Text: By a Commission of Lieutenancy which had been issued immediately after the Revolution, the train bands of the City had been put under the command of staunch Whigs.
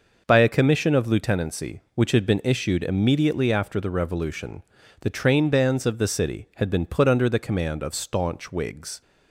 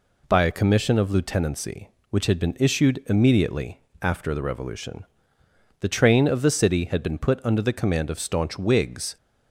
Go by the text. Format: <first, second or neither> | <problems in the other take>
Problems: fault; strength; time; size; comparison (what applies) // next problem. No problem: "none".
first | pauses between "immediately" and "after"; slight; at 3.8 s; 0.20 s long // skips "bands"; at 6.2 s